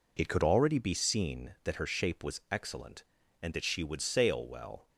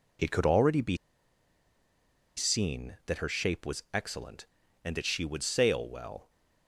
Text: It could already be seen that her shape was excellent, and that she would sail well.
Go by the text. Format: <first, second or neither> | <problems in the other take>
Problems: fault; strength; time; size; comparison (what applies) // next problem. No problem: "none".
first | pauses between "be" and "seen"; strong; at 0.9 s; 1.4 s long